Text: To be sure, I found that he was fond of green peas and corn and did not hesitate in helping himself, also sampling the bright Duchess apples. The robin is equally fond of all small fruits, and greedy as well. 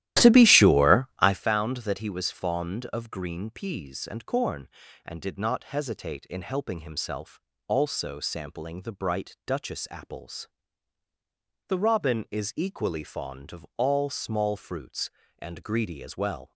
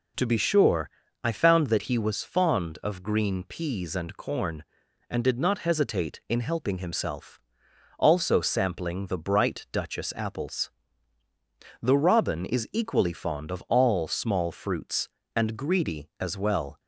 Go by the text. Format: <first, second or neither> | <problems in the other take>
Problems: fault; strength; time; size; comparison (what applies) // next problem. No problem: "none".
second | starts louder than the rest; strong; until 1.4 s; 14 dB